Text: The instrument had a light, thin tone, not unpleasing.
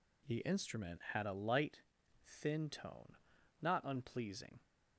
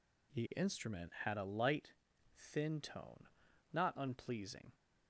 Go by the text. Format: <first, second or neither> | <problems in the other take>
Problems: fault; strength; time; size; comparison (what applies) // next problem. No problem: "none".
neither | none